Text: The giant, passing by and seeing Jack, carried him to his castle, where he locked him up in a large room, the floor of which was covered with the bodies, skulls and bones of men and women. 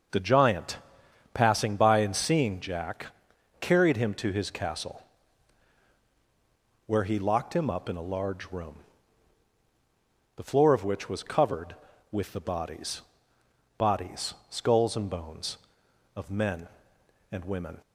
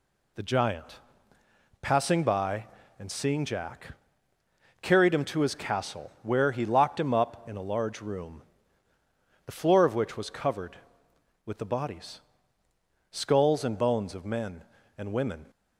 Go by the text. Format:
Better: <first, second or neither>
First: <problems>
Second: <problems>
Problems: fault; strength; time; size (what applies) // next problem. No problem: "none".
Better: second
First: starts louder than the rest; until 1.6 s; 6 dB // says "bodies" twice; at 13.7 s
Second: none